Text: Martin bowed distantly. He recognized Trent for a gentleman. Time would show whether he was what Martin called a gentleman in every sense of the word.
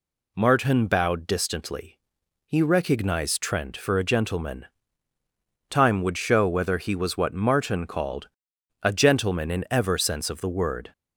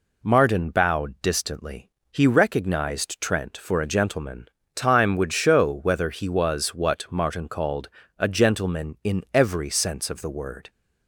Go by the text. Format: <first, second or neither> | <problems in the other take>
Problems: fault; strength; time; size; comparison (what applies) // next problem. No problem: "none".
second | pauses between "called" and "a"; noticeable; at 8.2 s; 0.54 s long; slight in the second // says "ever" for "every"; at 9.7 s